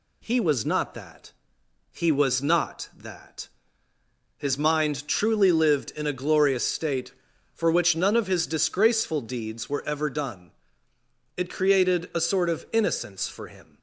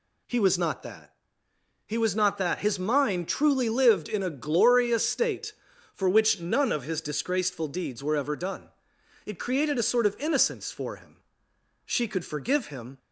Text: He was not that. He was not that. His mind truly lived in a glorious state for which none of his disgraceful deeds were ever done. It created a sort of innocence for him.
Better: first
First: none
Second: goes on to say "She could forgive him"; noticeable; from 11.8 s on; 1.1 s long

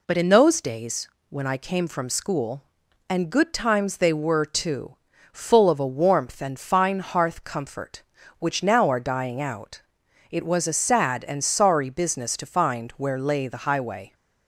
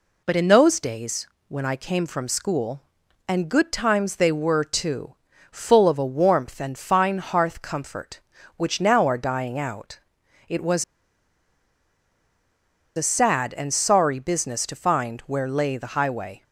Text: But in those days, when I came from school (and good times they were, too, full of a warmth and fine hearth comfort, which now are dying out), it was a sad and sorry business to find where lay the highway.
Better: first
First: none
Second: pauses between "was" and "a"; strong; at 10.8 s; 2.1 s long

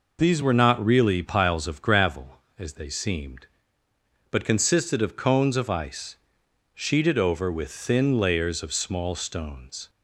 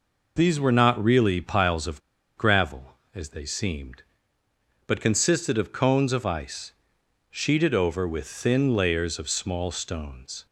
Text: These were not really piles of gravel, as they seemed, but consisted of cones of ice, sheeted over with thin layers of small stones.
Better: first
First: none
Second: pauses between "of" and "gravel"; at 1.9 s; 0.37 s long

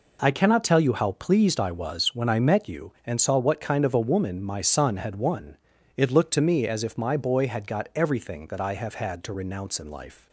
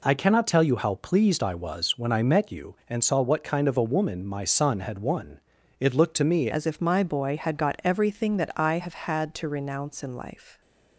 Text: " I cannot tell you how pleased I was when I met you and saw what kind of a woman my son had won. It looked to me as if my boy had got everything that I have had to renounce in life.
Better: first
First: none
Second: changes voice at "as"; from 6.4 s on; 4.2 s long

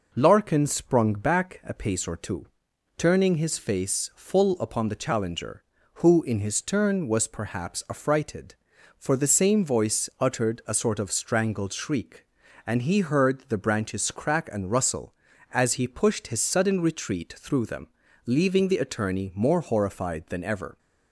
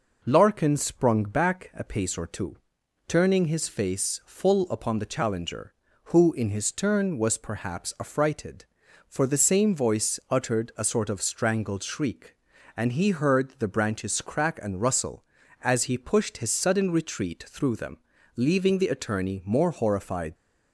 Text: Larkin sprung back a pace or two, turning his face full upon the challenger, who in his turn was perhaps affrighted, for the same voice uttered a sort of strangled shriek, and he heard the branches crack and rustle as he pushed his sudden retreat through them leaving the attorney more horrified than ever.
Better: first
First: pauses between "them" and "leaving"; slight; at 17.8 s; 0.36 s long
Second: pauses between "them" and "leaving"; slight; at 17.9 s; 0.36 s long // stops before "than ever"; at 20.3 s

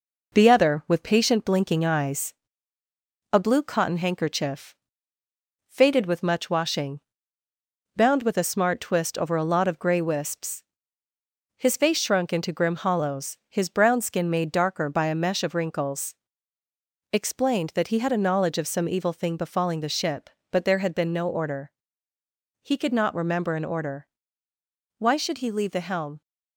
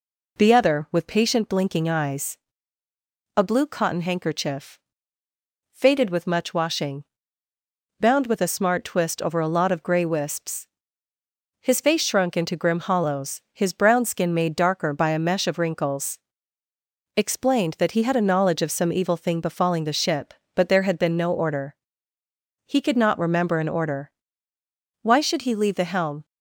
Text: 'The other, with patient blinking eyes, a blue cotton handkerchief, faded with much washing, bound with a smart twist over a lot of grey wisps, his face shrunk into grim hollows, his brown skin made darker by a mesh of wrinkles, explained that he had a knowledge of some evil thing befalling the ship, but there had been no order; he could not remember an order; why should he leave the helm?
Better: second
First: gets quieter; slight; throughout; 3.5 dB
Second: none

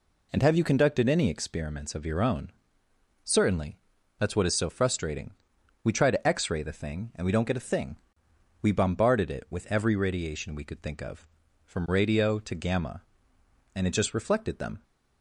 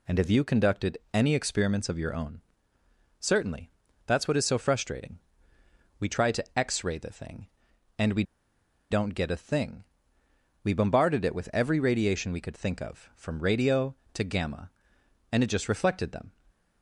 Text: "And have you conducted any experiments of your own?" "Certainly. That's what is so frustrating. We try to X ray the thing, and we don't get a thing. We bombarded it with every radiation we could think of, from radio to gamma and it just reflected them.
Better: first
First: none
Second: pauses between "we" and "don't"; noticeable; at 8.2 s; 0.68 s long

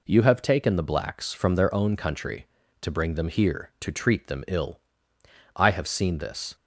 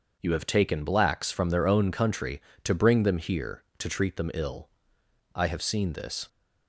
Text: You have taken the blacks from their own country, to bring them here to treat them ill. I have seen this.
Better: first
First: none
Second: skips "the"; at 0.8 s

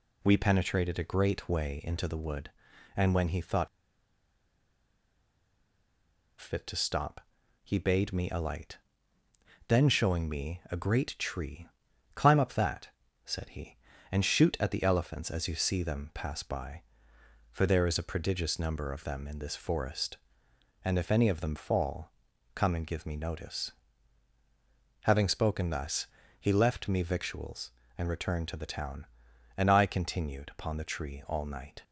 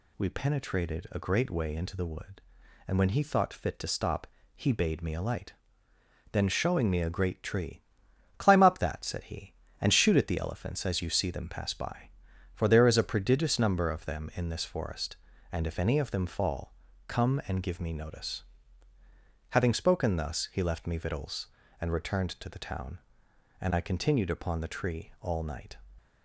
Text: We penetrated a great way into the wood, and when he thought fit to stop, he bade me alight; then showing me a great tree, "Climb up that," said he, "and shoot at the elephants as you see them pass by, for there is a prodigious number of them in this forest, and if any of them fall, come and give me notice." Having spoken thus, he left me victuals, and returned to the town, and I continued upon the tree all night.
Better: second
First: pauses between "thought" and "fit"; strong; at 3.6 s; 2.7 s long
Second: none

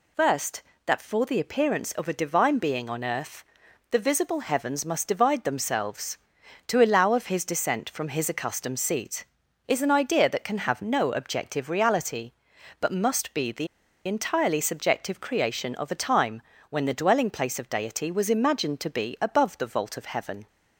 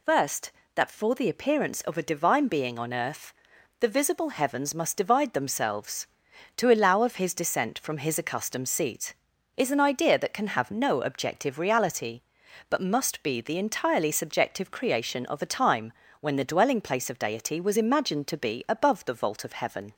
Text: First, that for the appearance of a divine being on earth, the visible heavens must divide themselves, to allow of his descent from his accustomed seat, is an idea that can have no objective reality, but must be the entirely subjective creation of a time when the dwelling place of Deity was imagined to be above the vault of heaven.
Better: second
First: pauses between "the" and "entirely"; at 13.6 s; 0.39 s long // pauses between "time" and "when"; slight; at 16.4 s; 0.30 s long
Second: pauses between "time" and "when"; slight; at 15.9 s; 0.30 s long

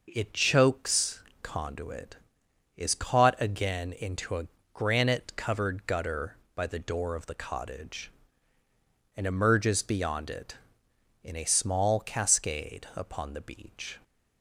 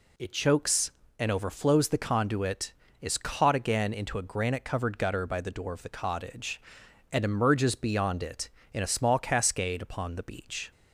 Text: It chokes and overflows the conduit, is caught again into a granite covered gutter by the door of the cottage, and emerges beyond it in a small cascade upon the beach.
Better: second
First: skips "and overflows the"; at 1.3 s // pauses between "a" and "granite"; slight; at 4.4 s; 0.30 s long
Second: none

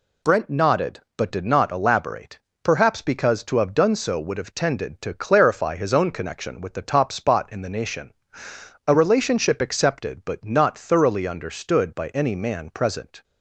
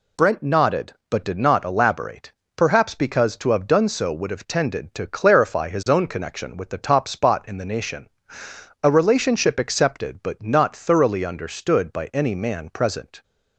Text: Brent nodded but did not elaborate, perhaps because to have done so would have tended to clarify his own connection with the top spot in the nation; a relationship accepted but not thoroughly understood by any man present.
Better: neither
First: none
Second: none

